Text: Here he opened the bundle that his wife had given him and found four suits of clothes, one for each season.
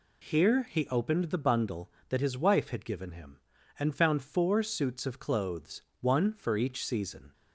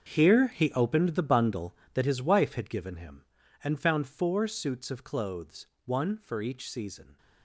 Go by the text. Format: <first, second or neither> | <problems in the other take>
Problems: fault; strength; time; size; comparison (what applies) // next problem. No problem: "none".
first | gets quieter; strong; throughout; 14 dB